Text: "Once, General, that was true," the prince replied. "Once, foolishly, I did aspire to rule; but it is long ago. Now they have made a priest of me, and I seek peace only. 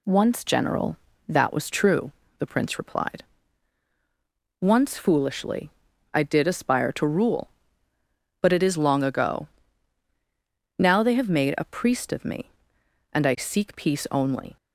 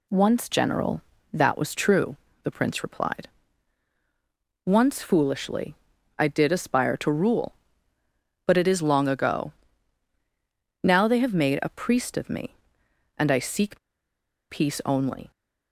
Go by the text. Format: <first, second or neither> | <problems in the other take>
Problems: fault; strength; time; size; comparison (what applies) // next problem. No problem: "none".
first | pauses between "seek" and "peace"; noticeable; at 13.7 s; 0.73 s long